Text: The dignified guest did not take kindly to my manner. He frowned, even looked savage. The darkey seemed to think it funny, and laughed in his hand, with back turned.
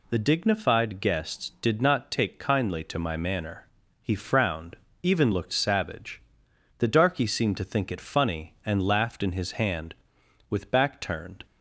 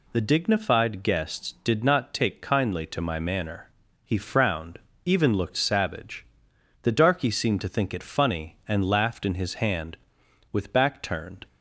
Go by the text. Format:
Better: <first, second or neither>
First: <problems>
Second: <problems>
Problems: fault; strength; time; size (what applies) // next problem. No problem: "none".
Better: neither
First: none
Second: none